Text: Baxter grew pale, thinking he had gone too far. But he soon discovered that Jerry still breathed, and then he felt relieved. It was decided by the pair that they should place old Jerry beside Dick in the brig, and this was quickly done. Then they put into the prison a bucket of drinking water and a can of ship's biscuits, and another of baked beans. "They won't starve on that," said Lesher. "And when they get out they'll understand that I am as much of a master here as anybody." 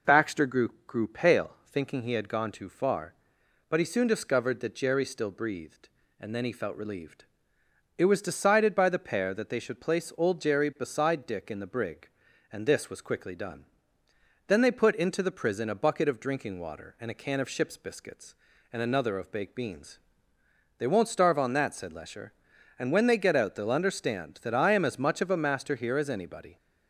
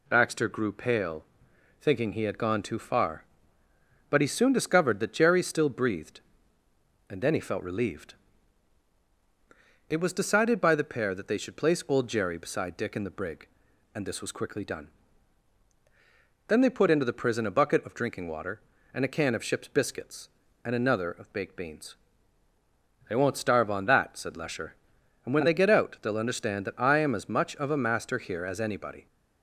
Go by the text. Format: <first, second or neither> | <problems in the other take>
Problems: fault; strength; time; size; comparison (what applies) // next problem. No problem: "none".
second | says "grew" twice; at 0.8 s